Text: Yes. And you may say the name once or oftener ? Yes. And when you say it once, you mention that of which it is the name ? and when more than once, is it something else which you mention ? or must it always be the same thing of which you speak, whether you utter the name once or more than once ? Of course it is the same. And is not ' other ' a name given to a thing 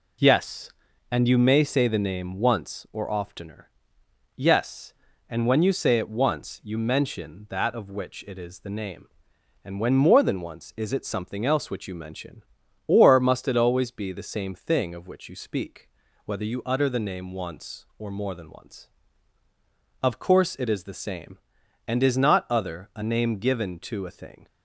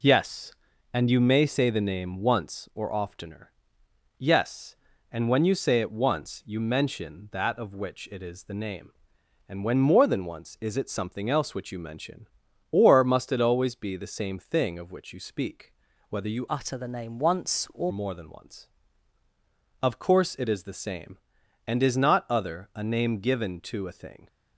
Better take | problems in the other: first | changes voice from "utter" to "or"; from 16.4 to 17.9 s; 1.5 s long

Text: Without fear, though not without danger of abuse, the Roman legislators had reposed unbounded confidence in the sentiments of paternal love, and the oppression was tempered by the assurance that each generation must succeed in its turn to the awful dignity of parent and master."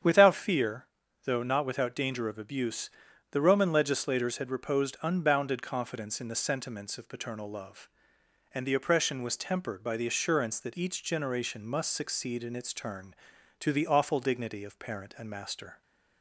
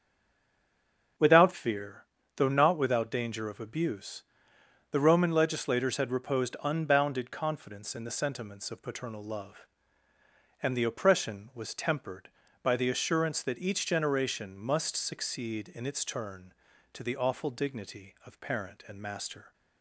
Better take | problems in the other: first | stays silent before the first word; noticeable; until 1.1 s; 1.1 s long // starts louder than the rest; until 2.5 s; 7 dB; strong in the first

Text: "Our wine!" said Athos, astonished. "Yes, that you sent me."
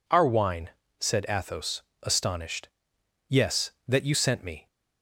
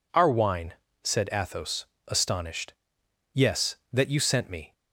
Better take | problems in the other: neither | none

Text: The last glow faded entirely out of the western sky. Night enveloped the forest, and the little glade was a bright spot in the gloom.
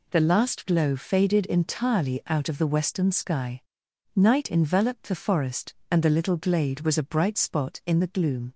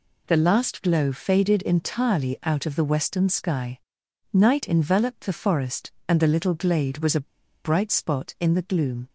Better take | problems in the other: first | pauses between "a" and "bright"; at 7.2 s; 0.38 s long

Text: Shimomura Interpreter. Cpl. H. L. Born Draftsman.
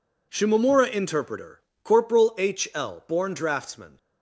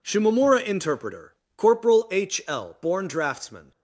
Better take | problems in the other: neither | none

